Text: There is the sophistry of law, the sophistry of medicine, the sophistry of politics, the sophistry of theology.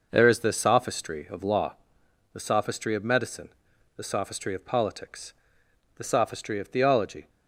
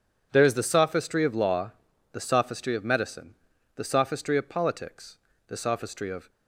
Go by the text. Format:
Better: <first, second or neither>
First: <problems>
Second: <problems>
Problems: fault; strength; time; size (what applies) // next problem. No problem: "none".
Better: first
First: none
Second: stops before "theology"; at 6.2 s